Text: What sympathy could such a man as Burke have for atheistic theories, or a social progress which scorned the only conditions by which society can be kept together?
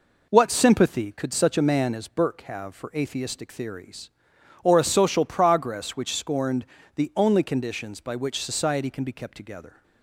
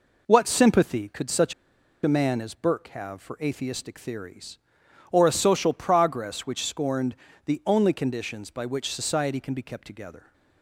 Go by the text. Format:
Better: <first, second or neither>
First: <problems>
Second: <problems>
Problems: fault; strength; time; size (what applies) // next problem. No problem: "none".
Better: first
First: pauses between "scorned" and "the"; slight; at 6.6 s; 0.30 s long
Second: pauses between "such" and "a"; noticeable; at 1.5 s; 0.50 s long // pauses between "scorned" and "the"; slight; at 7.1 s; 0.30 s long